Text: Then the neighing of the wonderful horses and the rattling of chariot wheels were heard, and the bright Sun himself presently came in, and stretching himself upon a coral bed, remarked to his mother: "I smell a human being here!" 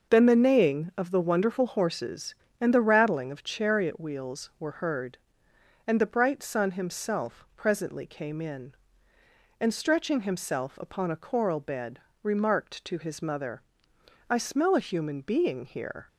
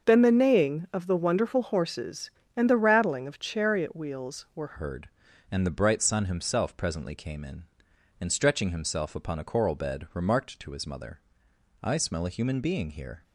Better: first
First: starts louder than the rest; noticeable; until 1.1 s; 6 dB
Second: starts louder than the rest; until 1.1 s; 6.5 dB // changes voice at "heard"; from 4.7 s on; 8.5 s long

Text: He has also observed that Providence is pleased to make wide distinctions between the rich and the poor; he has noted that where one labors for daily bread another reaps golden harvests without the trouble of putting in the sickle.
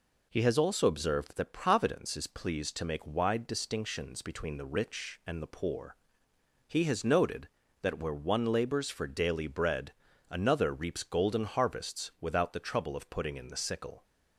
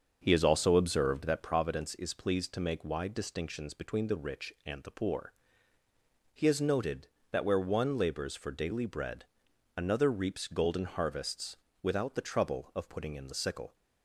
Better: first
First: pauses between "bread" and "another"; at 9.9 s; 0.38 s long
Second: starts louder than the rest; until 1.6 s; 6.5 dB // pauses between "bread" and "another"; noticeable; at 9.2 s; 0.52 s long // pauses between "harvests" and "without"; slight; at 11.5 s; 0.26 s long

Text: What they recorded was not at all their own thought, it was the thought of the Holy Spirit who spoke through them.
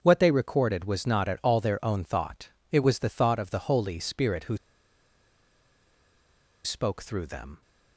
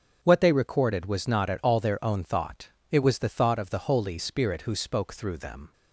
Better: second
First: starts louder than the rest; until 1.0 s; 6.5 dB // pauses between "who" and "spoke"; strong; at 4.5 s; 2.0 s long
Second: starts louder than the rest; until 1.2 s; 7 dB

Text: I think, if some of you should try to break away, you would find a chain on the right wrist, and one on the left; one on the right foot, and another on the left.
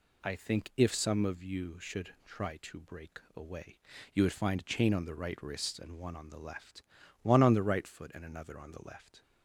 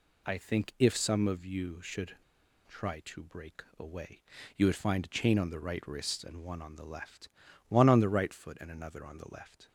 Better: first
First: pauses between "break" and "away"; slight; at 3.1 s; 0.16 s long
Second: pauses between "should" and "try"; noticeable; at 2.1 s; 0.52 s long // pauses between "break" and "away"; slight; at 3.6 s; 0.16 s long

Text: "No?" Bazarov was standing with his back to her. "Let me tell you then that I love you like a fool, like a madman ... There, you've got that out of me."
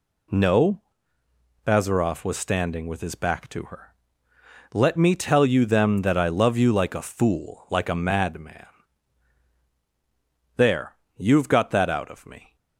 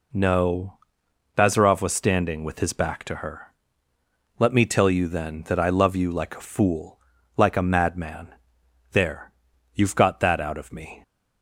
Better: second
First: says "them" for "then"; at 5.6 s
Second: none

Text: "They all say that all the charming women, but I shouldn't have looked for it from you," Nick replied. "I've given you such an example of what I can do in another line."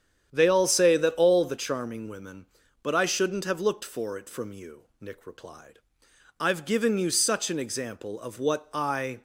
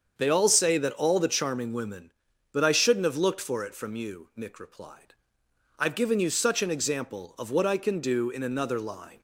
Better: second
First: starts louder than the rest; strong; until 1.3 s; 9 dB // stops before "can do in another line"; at 9.1 s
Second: starts louder than the rest; until 1.1 s; 7 dB

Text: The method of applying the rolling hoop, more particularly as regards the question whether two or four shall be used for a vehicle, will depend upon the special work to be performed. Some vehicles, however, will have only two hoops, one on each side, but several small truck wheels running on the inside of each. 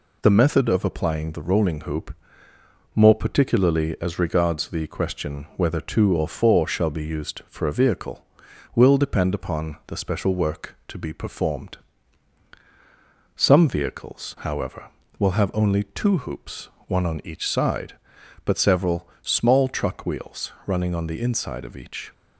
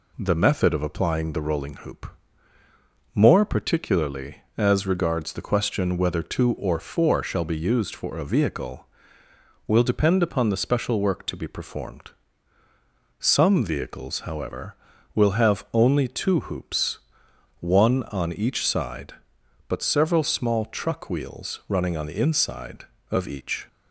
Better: neither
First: none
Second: none

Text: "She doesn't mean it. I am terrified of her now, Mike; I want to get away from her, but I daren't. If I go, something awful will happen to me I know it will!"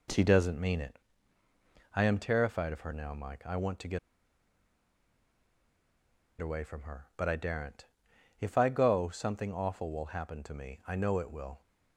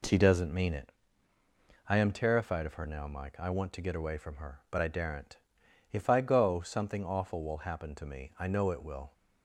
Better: second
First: pauses between "get" and "away"; strong; at 3.9 s; 2.4 s long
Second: none

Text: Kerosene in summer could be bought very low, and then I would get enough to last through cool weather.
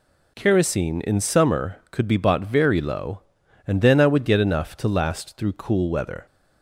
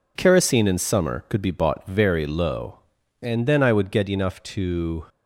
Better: first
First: none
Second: stops before "last through cool weather"; at 5.0 s

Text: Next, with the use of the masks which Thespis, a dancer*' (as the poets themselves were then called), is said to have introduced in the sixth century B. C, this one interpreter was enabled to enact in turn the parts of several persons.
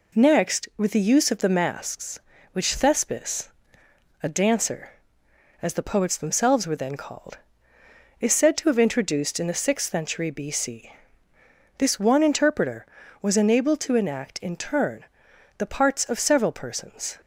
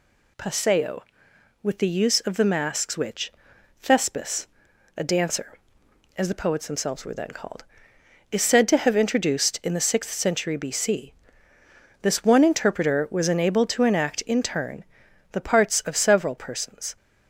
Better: first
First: pauses between "turn" and "the"; noticeable; at 15.0 s; 0.52 s long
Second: says "Paseo" for "Next"; at 0.3 s // pauses between "which" and "Thespis"; noticeable; at 3.3 s; 0.48 s long // pauses between "turn" and "the"; noticeable; at 14.8 s; 0.50 s long

